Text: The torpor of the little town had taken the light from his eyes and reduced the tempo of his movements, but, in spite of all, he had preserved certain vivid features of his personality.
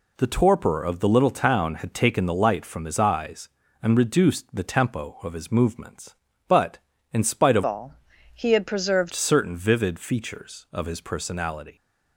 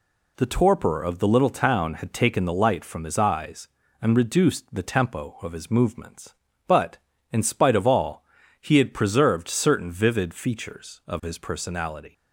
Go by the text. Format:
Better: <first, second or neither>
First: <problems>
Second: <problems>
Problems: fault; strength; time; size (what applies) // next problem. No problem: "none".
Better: second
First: changes voice from "all" to "preserved"; from 7.6 to 9.1 s; 1.5 s long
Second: none